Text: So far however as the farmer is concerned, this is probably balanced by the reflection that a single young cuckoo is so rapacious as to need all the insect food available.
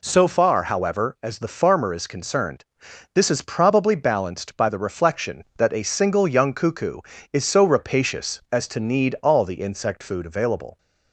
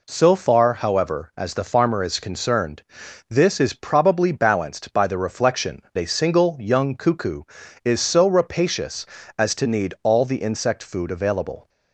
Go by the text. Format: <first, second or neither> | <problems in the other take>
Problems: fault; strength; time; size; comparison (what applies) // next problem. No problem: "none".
first | skips "that"; at 5.8 s